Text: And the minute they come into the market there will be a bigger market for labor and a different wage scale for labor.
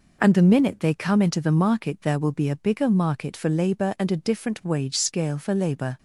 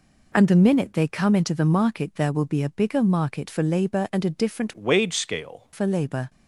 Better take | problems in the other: first | changes voice from "wage" to "scale"; from 4.7 to 5.6 s; 0.9 s long

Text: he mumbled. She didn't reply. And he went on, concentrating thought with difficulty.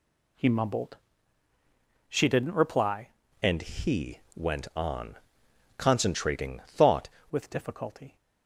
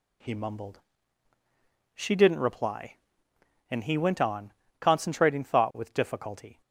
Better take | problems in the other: second | changes voice from "And" to "thought"; from 3.4 to 7.0 s; 3.6 s long // pauses between "he" and "went"; slight; at 4.1 s; 0.16 s long

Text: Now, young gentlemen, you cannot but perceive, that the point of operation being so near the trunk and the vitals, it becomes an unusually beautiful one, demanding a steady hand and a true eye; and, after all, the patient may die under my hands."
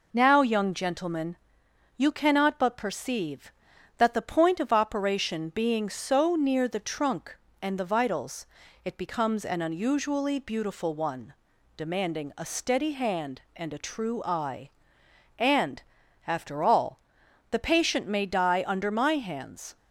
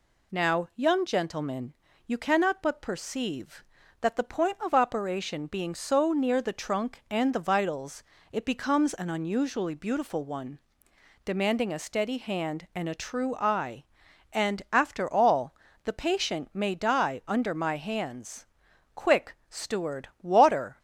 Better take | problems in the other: first | goes on to say "Quick Steward water"; strong; from 18.9 s on; 1.8 s long

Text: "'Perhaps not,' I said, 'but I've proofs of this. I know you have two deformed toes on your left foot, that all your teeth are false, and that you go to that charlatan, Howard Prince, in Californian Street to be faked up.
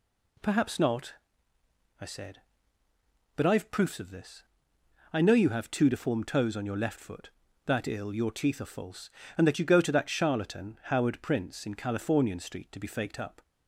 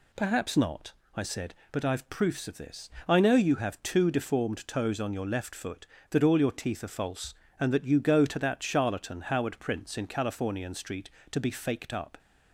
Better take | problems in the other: second | says "ill" for "all"; at 7.8 s

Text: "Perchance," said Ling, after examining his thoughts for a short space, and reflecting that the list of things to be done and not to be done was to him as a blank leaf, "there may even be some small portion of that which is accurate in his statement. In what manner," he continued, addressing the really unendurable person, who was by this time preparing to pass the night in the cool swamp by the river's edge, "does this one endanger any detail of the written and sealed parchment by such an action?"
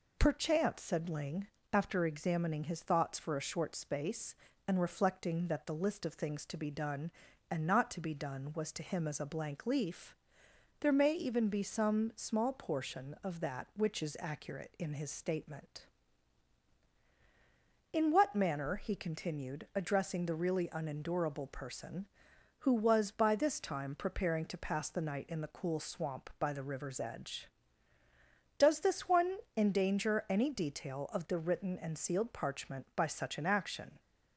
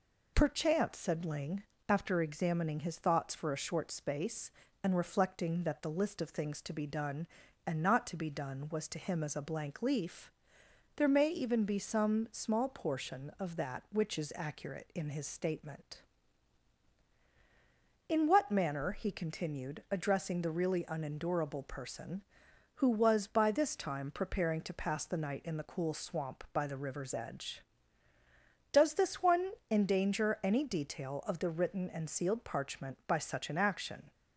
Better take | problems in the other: neither | pauses between "one" and "endanger"; slight; the same in both

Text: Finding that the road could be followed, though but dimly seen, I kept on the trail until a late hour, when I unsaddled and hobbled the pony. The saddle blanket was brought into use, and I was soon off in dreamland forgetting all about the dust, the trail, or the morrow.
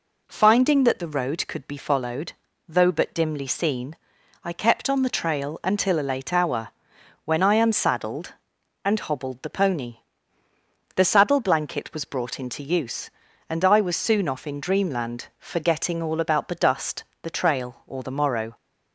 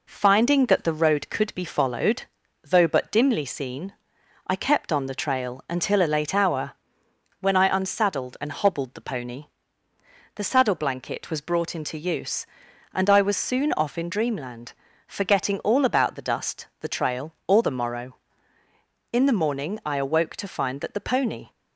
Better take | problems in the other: first | pauses between "dreamland" and "forgetting"; slight; at 14.7 s; 0.34 s long // goes on to say "In the morning I awoke to find that the pony"; strong; from 19.1 s on; 2.3 s long

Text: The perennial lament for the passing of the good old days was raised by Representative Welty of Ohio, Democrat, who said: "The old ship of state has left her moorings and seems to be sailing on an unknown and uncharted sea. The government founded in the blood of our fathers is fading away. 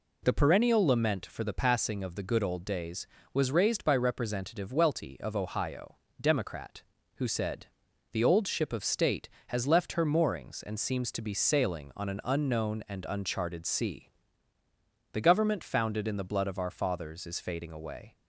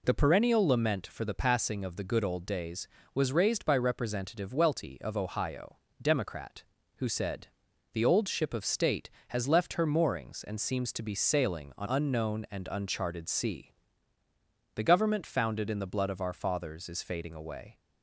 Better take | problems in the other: first | skips "an"; at 11.8 s

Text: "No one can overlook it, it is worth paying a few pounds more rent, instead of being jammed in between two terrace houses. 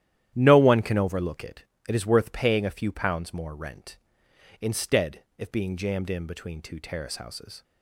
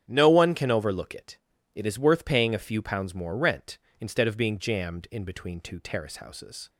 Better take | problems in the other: second | starts louder than the rest; strong; until 1.3 s; 11.5 dB; strong in the second // says "if" for "of"; at 5.3 s

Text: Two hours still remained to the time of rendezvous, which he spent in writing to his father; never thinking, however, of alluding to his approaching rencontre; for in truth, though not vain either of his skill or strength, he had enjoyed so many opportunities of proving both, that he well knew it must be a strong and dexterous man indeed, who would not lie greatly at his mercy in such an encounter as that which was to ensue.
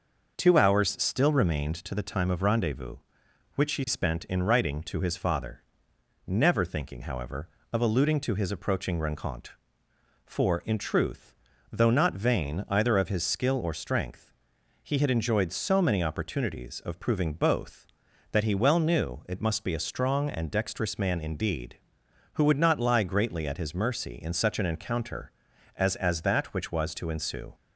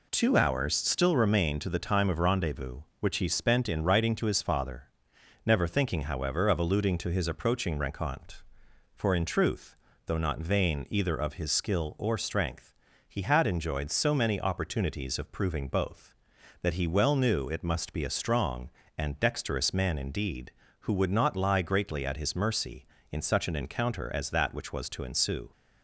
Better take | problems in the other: second | says "as" twice; at 25.9 s

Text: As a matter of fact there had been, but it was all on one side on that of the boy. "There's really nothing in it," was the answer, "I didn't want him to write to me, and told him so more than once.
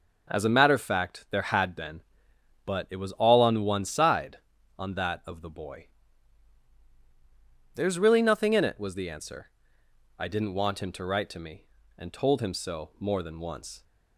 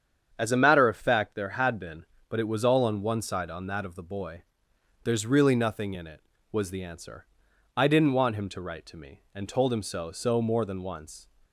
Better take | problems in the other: first | starts louder than the rest; strong; until 1.3 s; 8 dB // says "so" twice; at 10.1 s

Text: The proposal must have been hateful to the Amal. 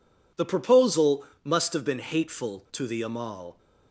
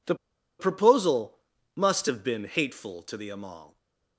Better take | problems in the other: first | pauses between "The" and "proposal"; at 0.1 s; 0.44 s long // pauses between "proposal" and "must"; slight; at 1.3 s; 0.36 s long; slight in the first // stays silent after the last word; slight; from 3.6 s on; 0.5 s long

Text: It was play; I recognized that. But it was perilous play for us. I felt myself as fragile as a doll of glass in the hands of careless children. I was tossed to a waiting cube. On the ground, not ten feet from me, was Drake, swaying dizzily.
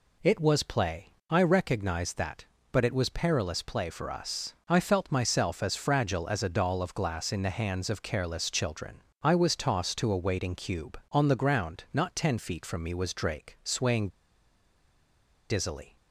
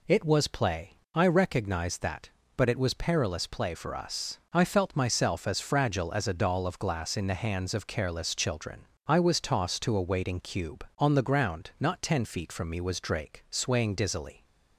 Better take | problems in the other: second | pauses between "swaying" and "dizzily"; strong; at 14.0 s; 1.4 s long

